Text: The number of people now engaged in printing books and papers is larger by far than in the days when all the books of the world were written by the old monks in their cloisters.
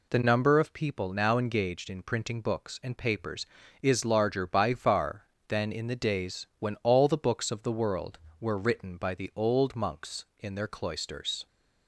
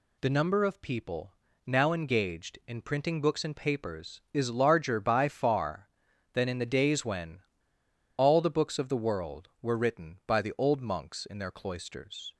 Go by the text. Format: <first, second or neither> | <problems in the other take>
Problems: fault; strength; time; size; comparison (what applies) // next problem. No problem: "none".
first | pauses between "people" and "now"; slight; at 1.3 s; 0.30 s long // pauses between "when" and "all"; noticeable; at 7.3 s; 0.80 s long